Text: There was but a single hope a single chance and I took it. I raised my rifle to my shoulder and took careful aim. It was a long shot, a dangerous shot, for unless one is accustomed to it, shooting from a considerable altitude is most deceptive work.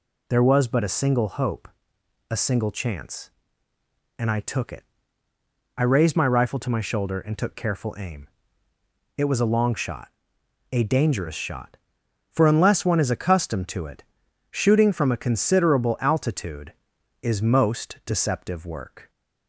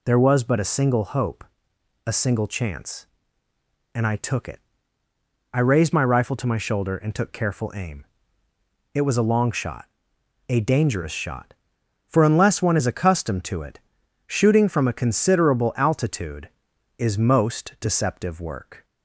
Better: neither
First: pauses between "hope" and "a"; noticeable; at 1.6 s; 0.64 s long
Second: pauses between "hope" and "a"; noticeable; at 1.4 s; 0.64 s long

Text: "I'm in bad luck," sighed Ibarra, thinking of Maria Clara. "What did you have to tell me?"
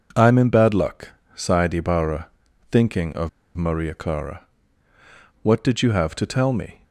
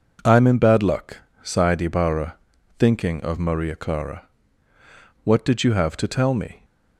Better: second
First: pauses between "of" and "Maria"; slight; at 3.2 s; 0.27 s long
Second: none

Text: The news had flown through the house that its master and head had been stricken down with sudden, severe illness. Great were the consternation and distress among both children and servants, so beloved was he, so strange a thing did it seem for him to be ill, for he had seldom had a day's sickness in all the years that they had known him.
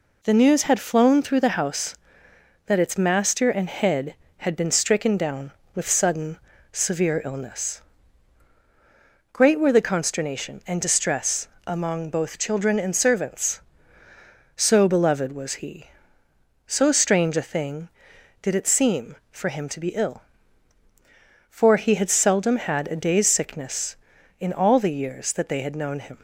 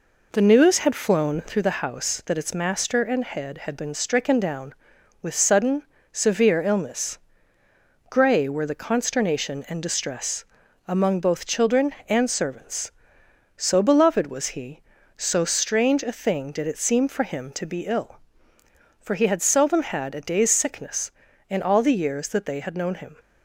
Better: first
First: pauses between "distress" and "among"; slight; at 11.4 s; 0.18 s long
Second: says "Grey" for "Great"; at 8.1 s // pauses between "distress" and "among"; at 10.4 s; 0.42 s long

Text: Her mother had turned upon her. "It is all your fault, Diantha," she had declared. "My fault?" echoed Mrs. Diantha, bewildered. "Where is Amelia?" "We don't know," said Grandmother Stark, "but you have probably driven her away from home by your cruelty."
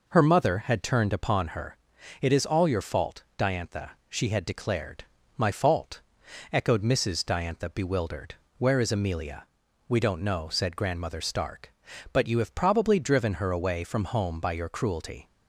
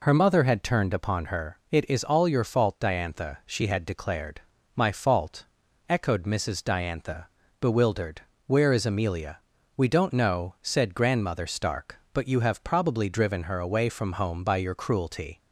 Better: neither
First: none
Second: none

